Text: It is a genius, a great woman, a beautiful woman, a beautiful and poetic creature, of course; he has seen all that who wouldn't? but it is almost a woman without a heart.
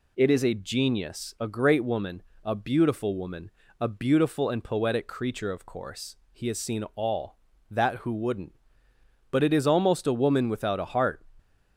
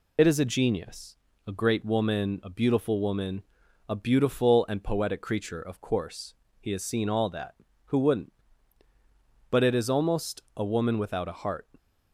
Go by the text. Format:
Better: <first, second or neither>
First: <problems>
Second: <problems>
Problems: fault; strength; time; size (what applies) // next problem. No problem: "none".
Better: first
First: none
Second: loses the start of "It"; at 0.1 s; 45 ms